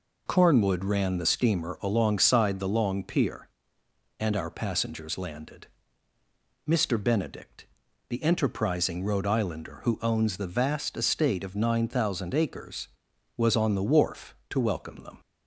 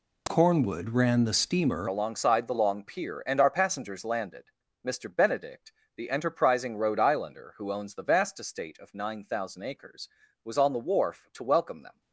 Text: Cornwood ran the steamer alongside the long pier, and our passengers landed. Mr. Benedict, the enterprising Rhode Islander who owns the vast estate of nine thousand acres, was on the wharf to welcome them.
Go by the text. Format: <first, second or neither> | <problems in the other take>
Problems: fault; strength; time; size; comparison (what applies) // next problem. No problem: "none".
first | changes voice at "alongside"; from 1.8 s on; 10.2 s long